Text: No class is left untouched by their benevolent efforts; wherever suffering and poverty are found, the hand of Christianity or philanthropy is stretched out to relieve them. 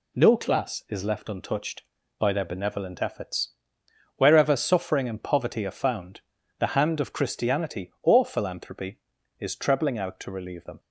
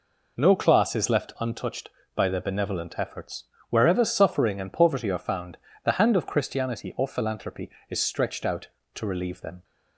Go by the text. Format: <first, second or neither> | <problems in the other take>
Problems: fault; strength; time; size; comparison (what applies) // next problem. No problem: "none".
second | says "trebling" for "stretched"; at 9.5 s